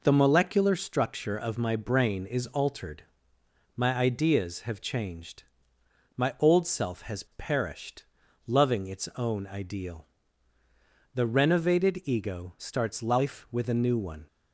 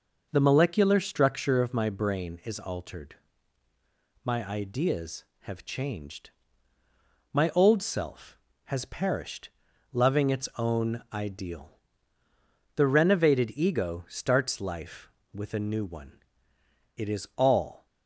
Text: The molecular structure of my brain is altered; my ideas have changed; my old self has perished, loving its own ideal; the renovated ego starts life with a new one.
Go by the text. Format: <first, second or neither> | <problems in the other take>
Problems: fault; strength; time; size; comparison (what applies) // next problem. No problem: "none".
first | goes on to say "It is all"; noticeable; from 16.9 s on; 0.88 s long